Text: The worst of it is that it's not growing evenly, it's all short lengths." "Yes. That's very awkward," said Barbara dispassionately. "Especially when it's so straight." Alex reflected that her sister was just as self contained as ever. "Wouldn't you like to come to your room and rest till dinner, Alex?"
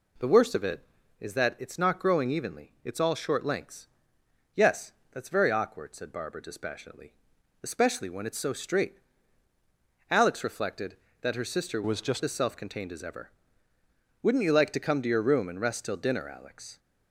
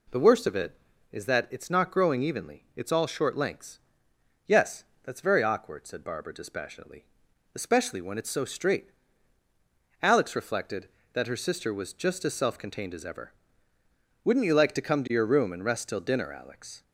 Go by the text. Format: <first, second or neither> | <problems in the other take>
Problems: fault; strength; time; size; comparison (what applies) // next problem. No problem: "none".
second | changes voice from "was" to "just"; from 11.8 to 12.2 s; 0.4 s long